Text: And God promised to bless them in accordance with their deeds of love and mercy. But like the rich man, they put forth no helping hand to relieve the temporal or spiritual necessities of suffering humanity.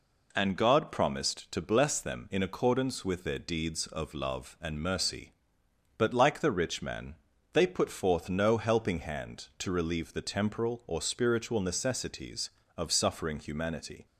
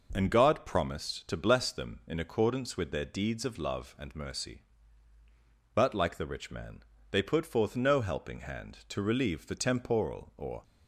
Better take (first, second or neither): first